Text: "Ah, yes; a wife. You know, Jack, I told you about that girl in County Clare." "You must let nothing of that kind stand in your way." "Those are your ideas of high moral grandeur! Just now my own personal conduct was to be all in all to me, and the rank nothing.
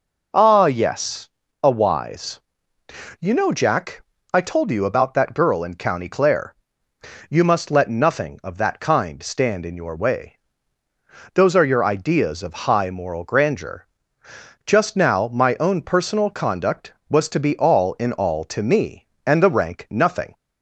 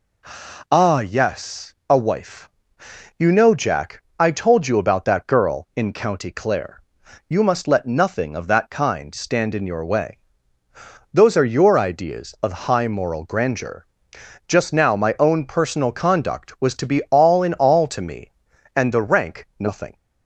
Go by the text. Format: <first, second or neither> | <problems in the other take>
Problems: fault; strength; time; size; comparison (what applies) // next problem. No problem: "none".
second | says "wise" for "wife"; at 1.6 s